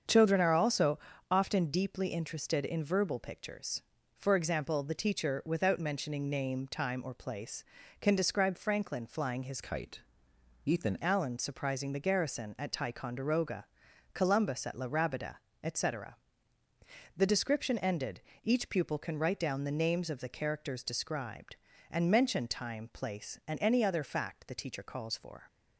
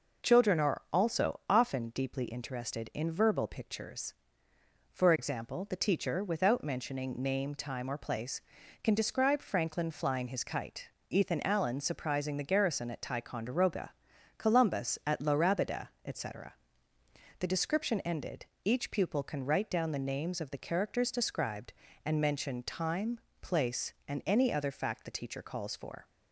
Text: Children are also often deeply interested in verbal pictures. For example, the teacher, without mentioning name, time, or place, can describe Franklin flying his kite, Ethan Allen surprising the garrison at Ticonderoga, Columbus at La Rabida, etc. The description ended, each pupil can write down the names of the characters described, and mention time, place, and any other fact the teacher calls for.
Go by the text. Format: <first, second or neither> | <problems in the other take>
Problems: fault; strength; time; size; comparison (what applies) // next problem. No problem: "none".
second | starts louder than the rest; strong; until 1.4 s; 7.5 dB // pauses between "also" and "often"; slight; at 0.9 s; 0.32 s long // changes voice from "kite" to "Ethan"; from 9.6 to 10.9 s; 1.3 s long